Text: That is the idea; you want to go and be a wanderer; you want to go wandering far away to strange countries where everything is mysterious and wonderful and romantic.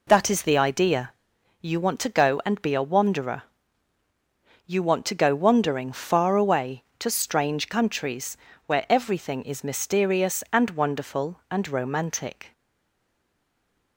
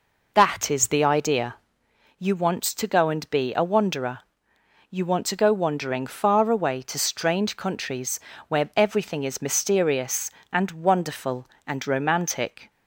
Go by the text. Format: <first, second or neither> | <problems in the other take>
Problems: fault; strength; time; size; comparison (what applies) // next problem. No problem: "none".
second | pauses between "countries" and "where"; slight; at 8.3 s; 0.26 s long; slight in the second // stays silent after the last word; noticeable; from 12.5 s on; 1.4 s long